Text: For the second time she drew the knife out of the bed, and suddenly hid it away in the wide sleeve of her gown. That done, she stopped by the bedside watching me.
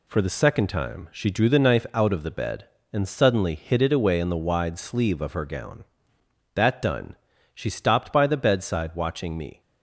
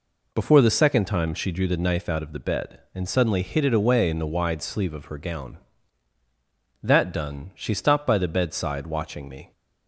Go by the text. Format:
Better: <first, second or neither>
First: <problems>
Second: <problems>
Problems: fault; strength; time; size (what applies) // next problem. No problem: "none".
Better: first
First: none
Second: says "Before" for "For"; at 0.3 s